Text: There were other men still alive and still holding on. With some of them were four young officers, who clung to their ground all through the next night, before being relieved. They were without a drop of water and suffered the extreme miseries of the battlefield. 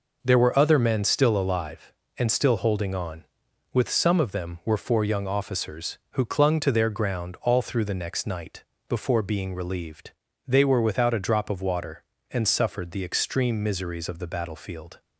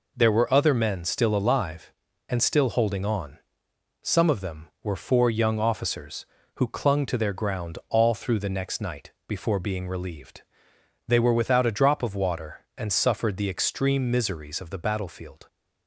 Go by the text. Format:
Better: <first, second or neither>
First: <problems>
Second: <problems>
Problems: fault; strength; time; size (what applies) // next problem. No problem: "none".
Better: first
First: none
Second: skips "With"; at 3.7 s